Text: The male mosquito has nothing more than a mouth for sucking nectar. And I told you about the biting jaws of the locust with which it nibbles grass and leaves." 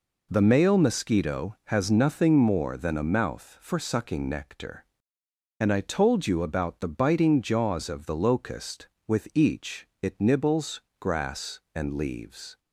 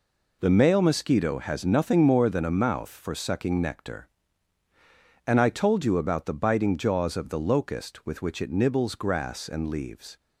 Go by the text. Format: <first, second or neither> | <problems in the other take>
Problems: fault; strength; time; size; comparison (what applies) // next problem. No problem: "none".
second | says "each" for "which"; at 9.3 s // pauses between "nibbles" and "grass"; slight; at 10.8 s; 0.20 s long